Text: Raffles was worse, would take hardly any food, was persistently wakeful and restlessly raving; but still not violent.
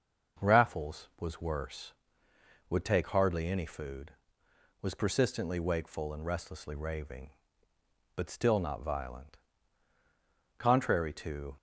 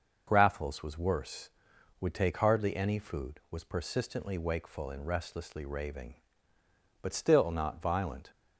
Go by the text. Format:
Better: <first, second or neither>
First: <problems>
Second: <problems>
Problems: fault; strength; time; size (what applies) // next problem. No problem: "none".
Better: second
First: starts louder than the rest; noticeable; until 1.5 s; 6 dB // goes on to say "Contrary to"; noticeable; from 10.5 s on; 0.96 s long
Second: none